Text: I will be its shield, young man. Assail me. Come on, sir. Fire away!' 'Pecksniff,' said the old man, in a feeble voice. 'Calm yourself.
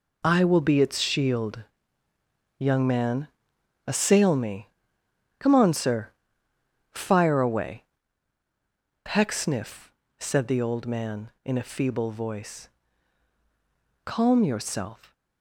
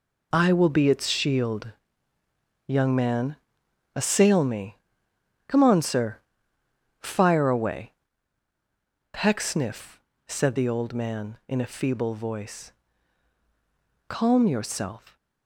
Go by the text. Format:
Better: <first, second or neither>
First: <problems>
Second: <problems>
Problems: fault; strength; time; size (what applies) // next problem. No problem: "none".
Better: neither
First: none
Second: none